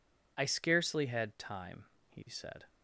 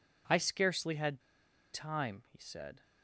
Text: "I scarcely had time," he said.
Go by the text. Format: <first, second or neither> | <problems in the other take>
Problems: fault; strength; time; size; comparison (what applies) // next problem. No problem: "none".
first | pauses between "had" and "time"; noticeable; at 1.2 s; 0.53 s long